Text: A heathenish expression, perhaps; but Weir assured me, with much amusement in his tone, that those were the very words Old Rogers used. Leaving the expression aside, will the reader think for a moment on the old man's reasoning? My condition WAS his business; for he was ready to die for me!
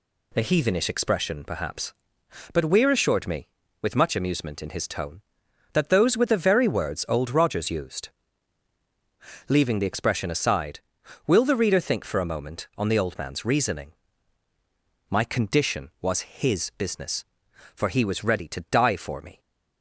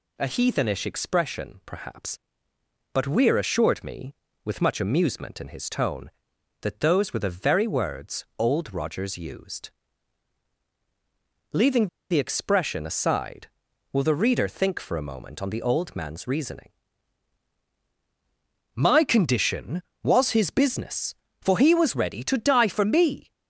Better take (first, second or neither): first